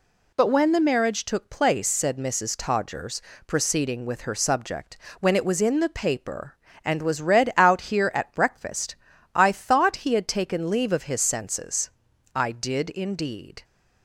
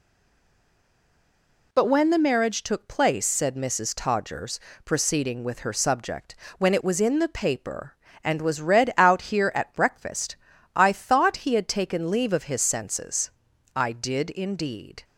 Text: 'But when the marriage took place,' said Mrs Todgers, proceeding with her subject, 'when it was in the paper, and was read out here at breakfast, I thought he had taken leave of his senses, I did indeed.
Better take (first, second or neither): first